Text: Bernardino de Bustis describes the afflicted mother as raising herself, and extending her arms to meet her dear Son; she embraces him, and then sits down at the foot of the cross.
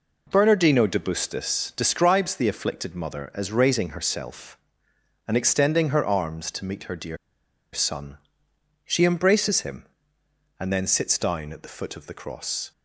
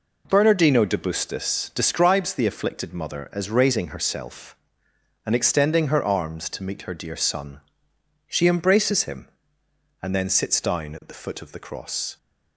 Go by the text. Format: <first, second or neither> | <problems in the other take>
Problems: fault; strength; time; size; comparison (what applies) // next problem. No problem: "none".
second | pauses between "dear" and "Son"; noticeable; at 7.1 s; 0.56 s long